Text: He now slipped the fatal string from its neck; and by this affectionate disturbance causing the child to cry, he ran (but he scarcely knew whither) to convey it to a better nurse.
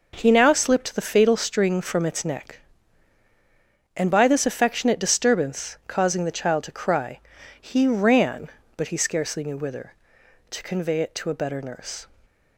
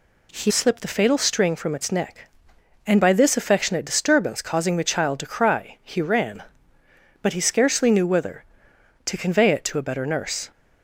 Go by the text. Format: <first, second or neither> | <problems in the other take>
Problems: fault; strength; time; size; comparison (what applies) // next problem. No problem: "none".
first | skips "now"; at 0.5 s